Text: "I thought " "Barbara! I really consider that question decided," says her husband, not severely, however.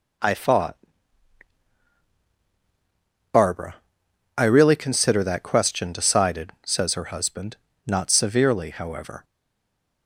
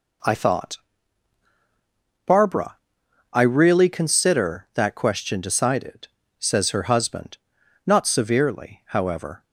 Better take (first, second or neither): second